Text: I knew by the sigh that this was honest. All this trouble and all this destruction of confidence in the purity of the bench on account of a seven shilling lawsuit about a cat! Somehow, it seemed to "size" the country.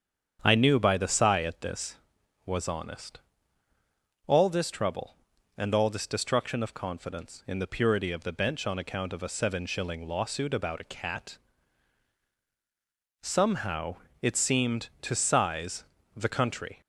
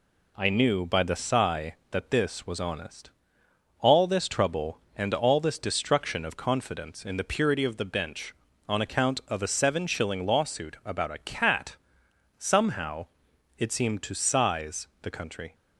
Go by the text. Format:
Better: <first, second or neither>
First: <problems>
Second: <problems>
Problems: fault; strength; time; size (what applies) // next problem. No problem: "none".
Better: second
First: starts louder than the rest; strong; until 1.4 s; 8 dB // says "at" for "that"; at 1.4 s // pauses between "size" and "the"; slight; at 15.8 s; 0.32 s long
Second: pauses between "size" and "the"; slight; at 14.8 s; 0.16 s long